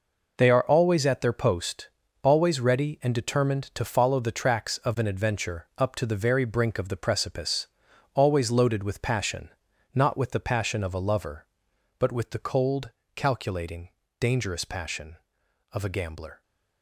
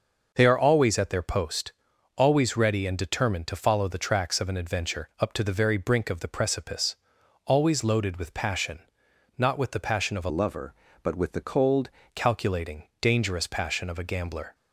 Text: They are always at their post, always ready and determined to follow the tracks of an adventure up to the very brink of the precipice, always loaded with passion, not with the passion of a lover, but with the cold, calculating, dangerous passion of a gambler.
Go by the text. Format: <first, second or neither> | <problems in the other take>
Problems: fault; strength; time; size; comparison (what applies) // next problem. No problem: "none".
first | changes voice from "lover" to "cold"; from 10.2 to 11.9 s; 1.7 s long